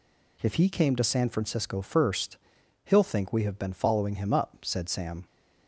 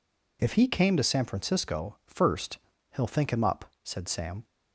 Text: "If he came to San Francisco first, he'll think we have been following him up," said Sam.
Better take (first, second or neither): first